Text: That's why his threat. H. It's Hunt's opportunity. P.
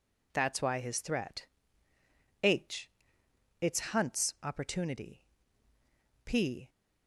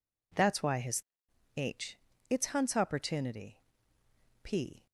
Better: first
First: none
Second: skips "threat"; at 1.2 s

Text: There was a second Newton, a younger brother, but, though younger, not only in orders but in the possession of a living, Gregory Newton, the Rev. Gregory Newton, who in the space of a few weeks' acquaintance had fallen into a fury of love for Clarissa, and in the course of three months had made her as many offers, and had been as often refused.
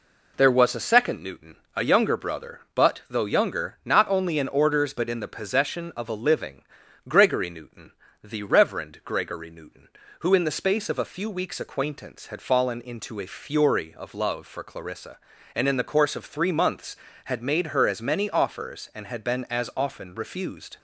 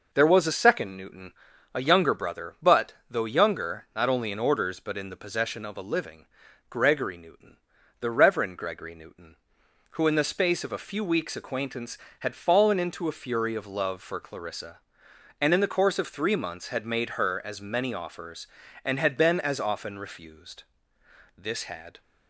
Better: first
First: none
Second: goes on to say "This had"; noticeable; from 21.3 s on; 0.64 s long

